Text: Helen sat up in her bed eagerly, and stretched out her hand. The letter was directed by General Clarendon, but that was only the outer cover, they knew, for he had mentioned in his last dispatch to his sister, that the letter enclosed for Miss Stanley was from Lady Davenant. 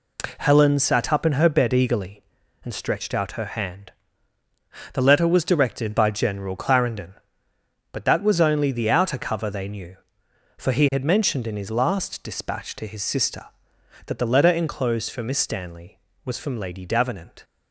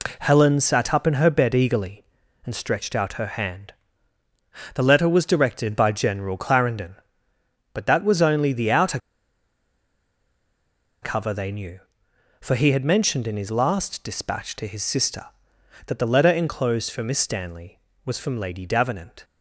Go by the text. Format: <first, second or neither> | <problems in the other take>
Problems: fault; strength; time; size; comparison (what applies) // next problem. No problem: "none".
first | pauses between "outer" and "cover"; strong; at 8.9 s; 2.0 s long